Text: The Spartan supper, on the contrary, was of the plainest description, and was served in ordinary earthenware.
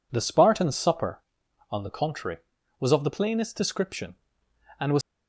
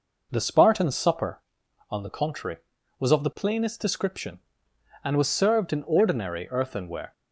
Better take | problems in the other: second | stops before "served in ordinary earthenware"; at 5.0 s

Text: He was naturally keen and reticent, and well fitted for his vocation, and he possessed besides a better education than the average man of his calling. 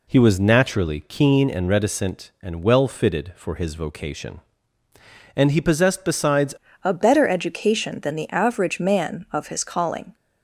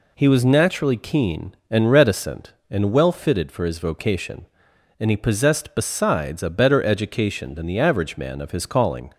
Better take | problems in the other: second | changes voice at "a"; from 6.8 s on; 3.3 s long

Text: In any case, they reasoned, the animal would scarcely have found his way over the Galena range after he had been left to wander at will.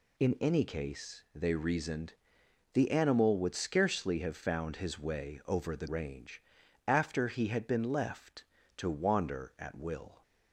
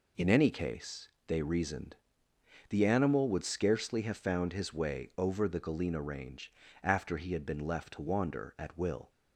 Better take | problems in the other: second | skips "Galena"; at 5.8 s // pauses between "range" and "after"; noticeable; at 6.4 s; 0.46 s long; slight in the second

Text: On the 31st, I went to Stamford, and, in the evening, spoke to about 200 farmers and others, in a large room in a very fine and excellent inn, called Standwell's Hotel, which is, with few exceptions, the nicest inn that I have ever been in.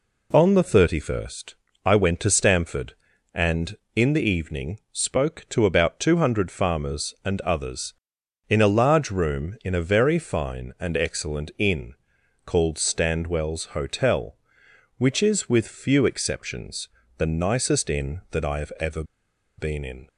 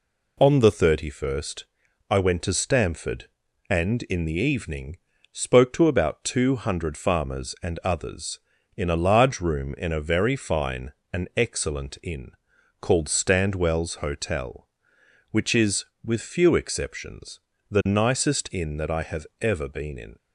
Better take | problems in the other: second | pauses between "ever" and "been"; noticeable; at 19.0 s; 0.54 s long

